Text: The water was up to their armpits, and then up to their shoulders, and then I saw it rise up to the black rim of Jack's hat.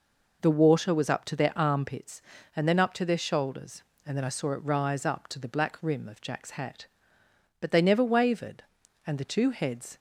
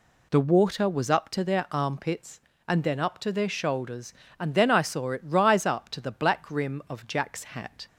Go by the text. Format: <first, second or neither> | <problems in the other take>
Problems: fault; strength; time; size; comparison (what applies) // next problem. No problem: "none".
second | goes on to say "But they never wavered and the two heads"; strong; from 7.5 s on; 2.3 s long